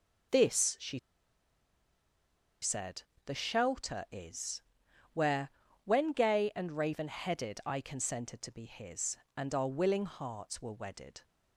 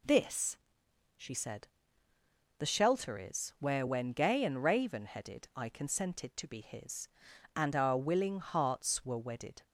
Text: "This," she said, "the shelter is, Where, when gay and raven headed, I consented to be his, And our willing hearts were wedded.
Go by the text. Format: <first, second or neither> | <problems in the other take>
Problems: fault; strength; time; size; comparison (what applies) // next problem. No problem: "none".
second | pauses between "she" and "said"; strong; at 0.9 s; 1.6 s long